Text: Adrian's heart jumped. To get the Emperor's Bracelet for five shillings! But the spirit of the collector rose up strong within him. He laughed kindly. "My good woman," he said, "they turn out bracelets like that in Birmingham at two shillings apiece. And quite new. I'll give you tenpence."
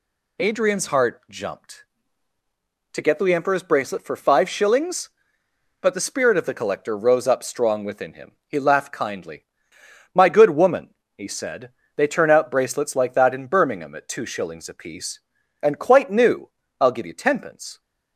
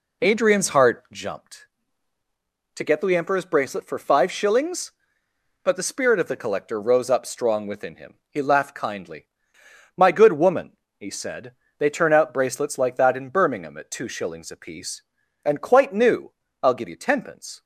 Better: first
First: none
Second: starts louder than the rest; slight; until 1.3 s; 2.5 dB

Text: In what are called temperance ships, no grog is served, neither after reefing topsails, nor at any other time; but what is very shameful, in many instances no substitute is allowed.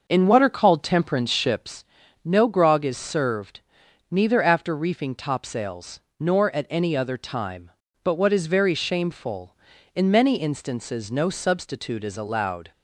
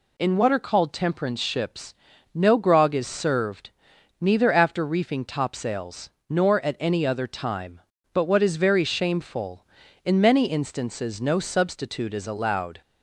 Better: second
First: starts louder than the rest; noticeable; until 1.8 s; 6 dB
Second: none

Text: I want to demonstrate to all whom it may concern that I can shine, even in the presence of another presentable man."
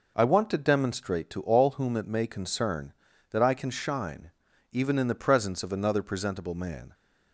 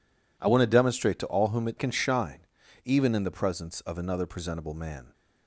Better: first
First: none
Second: skips "may concern that I"; at 1.7 s

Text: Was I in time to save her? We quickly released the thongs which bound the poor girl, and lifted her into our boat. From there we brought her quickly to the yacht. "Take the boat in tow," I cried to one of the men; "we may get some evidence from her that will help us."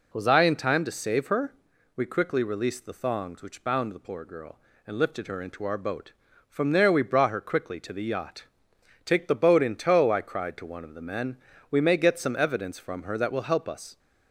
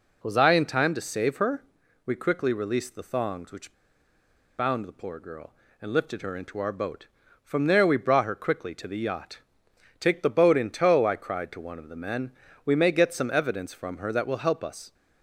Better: first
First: none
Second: pauses between "which" and "bound"; noticeable; at 3.7 s; 0.85 s long

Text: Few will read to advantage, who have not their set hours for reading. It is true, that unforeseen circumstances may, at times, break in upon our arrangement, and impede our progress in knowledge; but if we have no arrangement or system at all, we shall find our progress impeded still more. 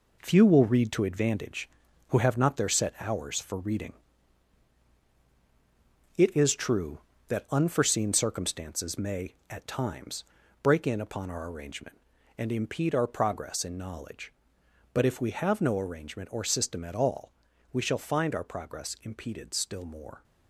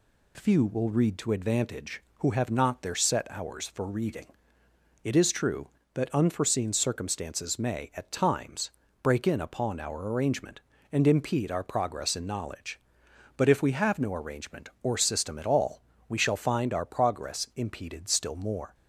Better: second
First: gets quieter; throughout; 7 dB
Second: none

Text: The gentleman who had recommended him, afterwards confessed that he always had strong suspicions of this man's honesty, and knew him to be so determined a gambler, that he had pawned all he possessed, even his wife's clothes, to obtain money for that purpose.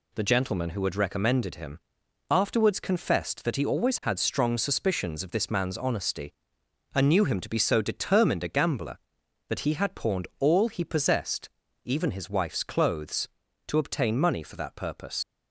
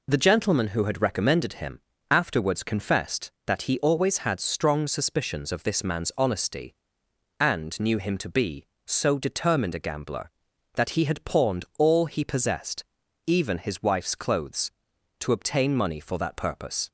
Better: second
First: leaves "purpose" unfinished; at 15.2 s; 95 ms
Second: none

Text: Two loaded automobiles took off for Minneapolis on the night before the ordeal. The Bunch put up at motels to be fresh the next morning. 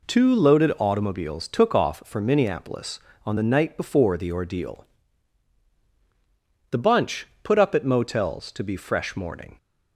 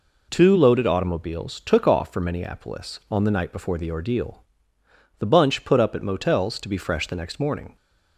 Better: second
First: pauses between "Bunch" and "put"; slight; at 7.2 s; 0.16 s long // skips "the next"; at 9.1 s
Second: none

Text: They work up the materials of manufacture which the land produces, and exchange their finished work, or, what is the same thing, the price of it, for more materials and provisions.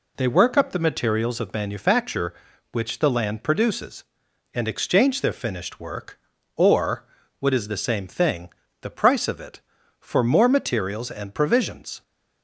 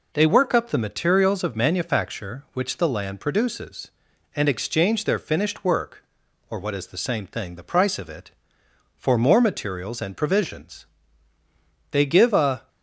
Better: first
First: none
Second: goes on to say "They give a"; noticeable; from 11.9 s on; 0.77 s long

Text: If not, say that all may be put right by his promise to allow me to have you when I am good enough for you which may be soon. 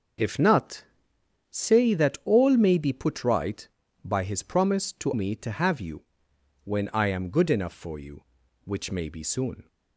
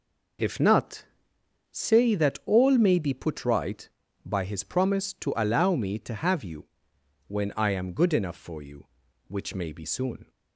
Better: second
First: starts louder than the rest; until 1.8 s; 6.5 dB // skips "allow"; at 5.1 s // pauses between "you" and "when"; noticeable; at 6.0 s; 0.64 s long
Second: pauses between "you" and "when"; noticeable; at 6.6 s; 0.64 s long

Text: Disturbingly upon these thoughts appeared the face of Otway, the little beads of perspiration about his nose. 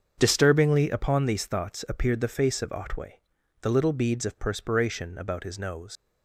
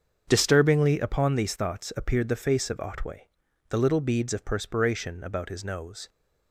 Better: second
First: starts louder than the rest; until 1.1 s; 7 dB // leaves "nose" unfinished; at 5.9 s; 80 ms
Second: starts louder than the rest; strong; until 1.2 s; 7 dB

